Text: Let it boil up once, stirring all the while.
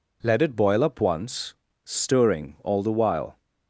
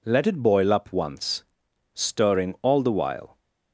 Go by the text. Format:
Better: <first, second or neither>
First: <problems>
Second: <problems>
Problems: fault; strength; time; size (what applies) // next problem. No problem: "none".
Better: neither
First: none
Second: none